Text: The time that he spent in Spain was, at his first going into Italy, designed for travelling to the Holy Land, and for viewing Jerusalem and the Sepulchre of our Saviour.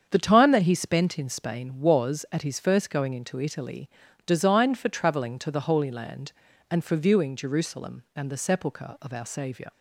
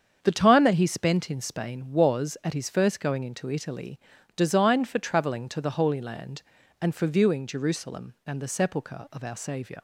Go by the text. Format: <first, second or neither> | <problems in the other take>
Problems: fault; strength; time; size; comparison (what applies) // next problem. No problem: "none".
neither | starts louder than the rest; strong; the same in both